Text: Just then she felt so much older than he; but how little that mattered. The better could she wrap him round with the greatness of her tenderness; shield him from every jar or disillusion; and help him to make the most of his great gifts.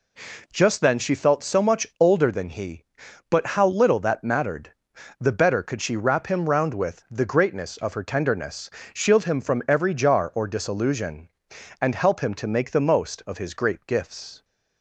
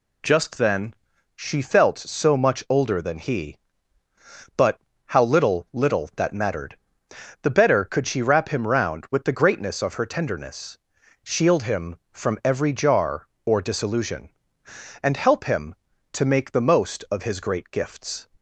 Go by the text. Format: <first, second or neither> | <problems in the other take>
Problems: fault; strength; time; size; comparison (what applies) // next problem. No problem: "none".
first | pauses between "then" and "she"; at 0.9 s; 0.42 s long // pauses between "but" and "how"; slight; at 4.8 s; 0.26 s long // says "little" twice; at 5.7 s